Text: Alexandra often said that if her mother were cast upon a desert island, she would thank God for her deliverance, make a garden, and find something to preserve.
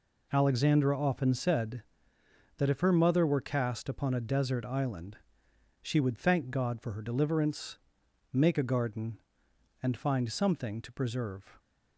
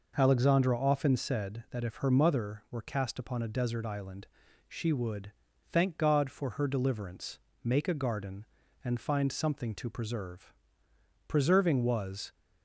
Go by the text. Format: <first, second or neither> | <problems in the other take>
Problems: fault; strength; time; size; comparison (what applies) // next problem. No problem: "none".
first | pauses between "would" and "thank"; at 5.3 s; 0.40 s long // goes on to say "Preserving was"; noticeable; from 11.2 s on; 1.0 s long